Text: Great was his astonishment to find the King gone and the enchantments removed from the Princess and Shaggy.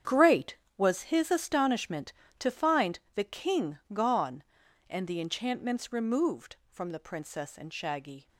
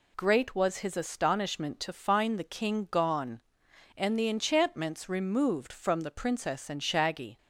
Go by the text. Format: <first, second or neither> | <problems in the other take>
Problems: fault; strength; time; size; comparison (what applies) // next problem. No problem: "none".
second | gets quieter; strong; throughout; 12.5 dB // pauses between "find" and "the"; slight; at 2.9 s; 0.16 s long